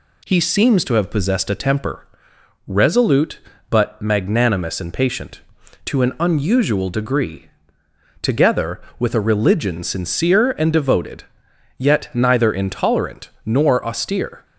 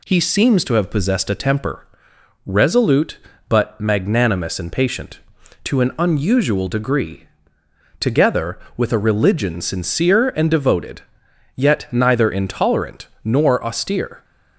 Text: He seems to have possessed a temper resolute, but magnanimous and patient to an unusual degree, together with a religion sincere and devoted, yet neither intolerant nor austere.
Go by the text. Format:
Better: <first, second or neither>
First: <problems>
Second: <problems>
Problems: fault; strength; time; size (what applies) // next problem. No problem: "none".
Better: neither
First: pauses between "temper" and "resolute"; noticeable; at 2.0 s; 0.60 s long // pauses between "intolerant" and "nor"; slight; at 13.2 s; 0.17 s long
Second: pauses between "temper" and "resolute"; noticeable; at 1.8 s; 0.58 s long // pauses between "intolerant" and "nor"; slight; at 13.0 s; 0.18 s long